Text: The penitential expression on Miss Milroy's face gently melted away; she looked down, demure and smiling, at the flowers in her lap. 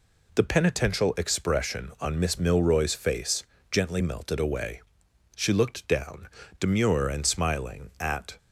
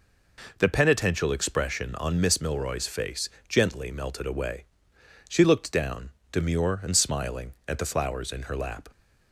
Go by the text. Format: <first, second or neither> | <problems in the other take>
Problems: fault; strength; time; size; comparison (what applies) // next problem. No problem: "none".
second | pauses between "face" and "gently"; slight; at 3.4 s; 0.26 s long; slight in the second // stops before "the flowers in her lap"; at 8.3 s